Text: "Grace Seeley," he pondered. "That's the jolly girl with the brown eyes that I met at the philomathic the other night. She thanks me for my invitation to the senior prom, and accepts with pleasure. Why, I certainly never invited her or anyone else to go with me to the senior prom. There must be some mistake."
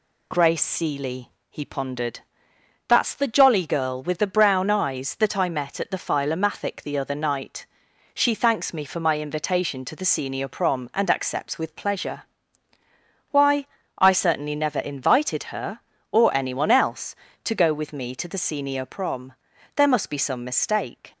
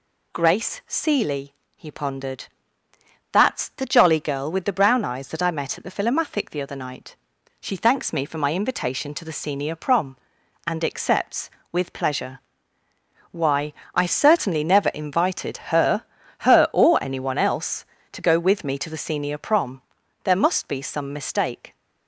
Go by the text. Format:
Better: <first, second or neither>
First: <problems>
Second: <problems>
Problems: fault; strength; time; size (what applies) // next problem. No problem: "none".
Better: first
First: none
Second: says "her" twice; at 16.3 s